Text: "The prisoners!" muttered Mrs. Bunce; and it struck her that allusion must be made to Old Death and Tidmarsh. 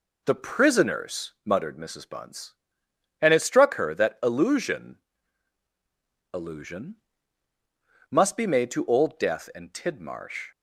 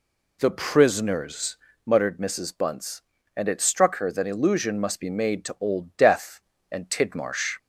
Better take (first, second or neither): second